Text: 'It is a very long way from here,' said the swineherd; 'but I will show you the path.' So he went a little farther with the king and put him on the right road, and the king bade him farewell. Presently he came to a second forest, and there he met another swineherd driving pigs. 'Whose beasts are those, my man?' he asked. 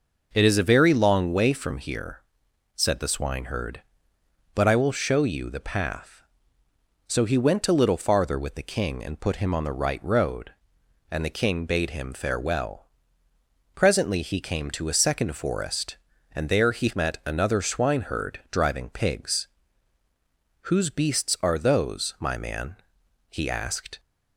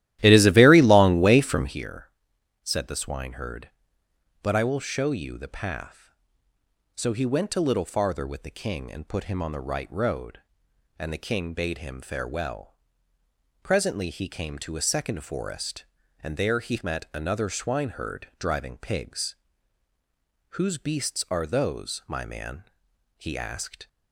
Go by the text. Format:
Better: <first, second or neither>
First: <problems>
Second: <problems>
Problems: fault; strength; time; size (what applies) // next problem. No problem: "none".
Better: first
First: none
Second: starts louder than the rest; strong; until 1.8 s; 14 dB